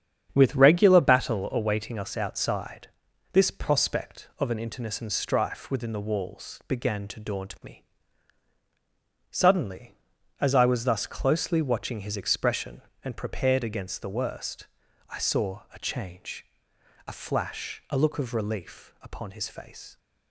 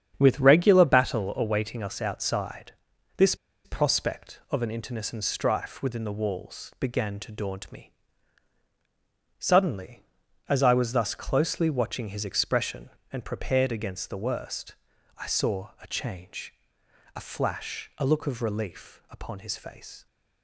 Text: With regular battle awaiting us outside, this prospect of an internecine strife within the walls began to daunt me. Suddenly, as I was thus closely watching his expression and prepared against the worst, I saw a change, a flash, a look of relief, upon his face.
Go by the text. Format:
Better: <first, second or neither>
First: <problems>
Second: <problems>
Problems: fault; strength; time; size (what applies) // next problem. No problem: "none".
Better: first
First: starts louder than the rest; strong; until 1.3 s; 8.5 dB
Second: starts louder than the rest; strong; until 1.1 s; 8.5 dB // pauses between "this" and "prospect"; slight; at 3.3 s; 0.29 s long